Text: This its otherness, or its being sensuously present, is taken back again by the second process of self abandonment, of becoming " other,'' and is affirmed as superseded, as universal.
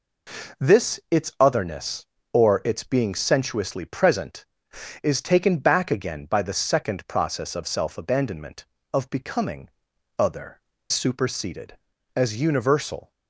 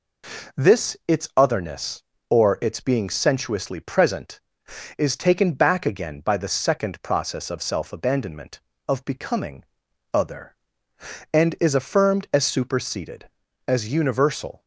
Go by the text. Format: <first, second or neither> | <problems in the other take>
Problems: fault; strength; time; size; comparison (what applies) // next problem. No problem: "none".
second | skips "and is affirmed as"; at 10.7 s